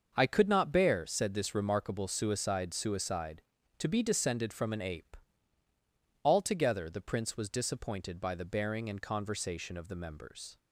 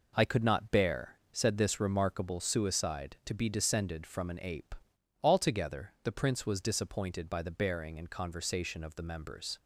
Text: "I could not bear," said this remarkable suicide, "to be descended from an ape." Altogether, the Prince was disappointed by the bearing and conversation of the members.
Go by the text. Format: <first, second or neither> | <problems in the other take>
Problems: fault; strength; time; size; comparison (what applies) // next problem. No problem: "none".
second | starts louder than the rest; until 1.1 s; 6.5 dB // says "suicide" twice; at 2.7 s